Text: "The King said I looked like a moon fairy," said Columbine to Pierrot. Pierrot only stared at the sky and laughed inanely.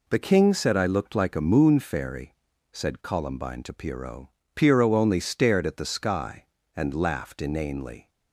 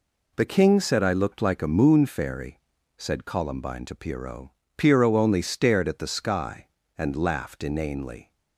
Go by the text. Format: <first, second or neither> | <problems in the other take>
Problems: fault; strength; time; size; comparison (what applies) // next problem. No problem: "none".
neither | none